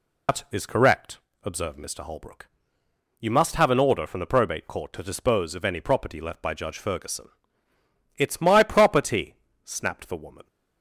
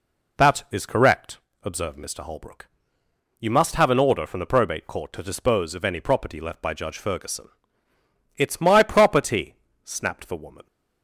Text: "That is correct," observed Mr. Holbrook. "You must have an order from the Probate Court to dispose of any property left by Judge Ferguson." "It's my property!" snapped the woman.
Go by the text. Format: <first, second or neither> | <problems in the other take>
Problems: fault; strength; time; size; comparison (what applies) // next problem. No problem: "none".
second | loses the start of "That"; at 0.2 s; 105 ms